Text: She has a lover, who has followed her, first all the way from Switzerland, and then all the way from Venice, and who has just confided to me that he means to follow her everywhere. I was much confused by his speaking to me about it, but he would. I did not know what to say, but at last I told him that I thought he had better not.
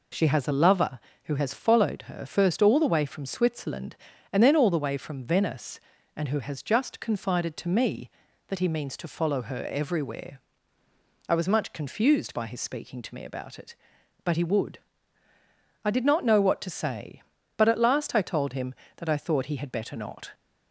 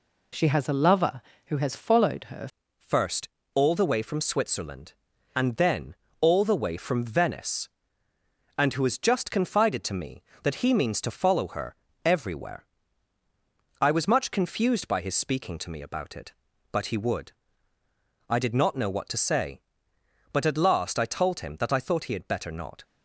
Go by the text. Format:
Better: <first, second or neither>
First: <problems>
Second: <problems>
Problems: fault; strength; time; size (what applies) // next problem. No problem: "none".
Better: first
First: none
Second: changes voice at "first"; from 2.7 s on; 20.1 s long // pauses between "first" and "all"; slight; at 3.2 s; 0.24 s long // pauses between "then" and "all"; slight; at 5.9 s; 0.24 s long // pauses between "her" and "everywhere"; slight; at 11.7 s; 0.28 s long